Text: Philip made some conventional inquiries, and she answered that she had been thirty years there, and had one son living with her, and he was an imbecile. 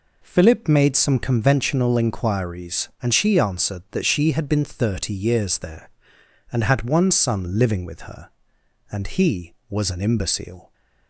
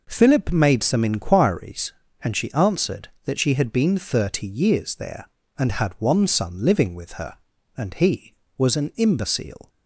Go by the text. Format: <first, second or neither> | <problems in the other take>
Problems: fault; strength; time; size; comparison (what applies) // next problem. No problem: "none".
first | skips "conventional"; at 1.0 s